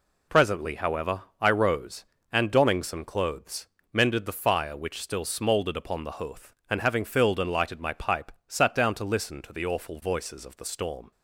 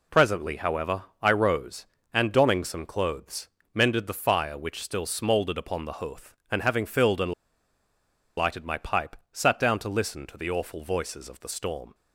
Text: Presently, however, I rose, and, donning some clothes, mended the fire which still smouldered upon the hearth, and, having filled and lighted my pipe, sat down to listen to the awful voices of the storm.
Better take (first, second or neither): first